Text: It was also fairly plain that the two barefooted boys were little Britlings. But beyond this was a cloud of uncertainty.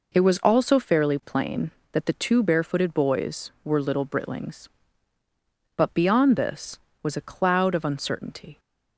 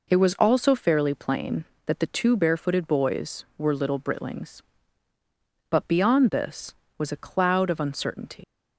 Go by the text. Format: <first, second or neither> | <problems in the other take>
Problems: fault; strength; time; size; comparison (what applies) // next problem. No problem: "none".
first | leaves "uncertainty" unfinished; at 8.4 s; 105 ms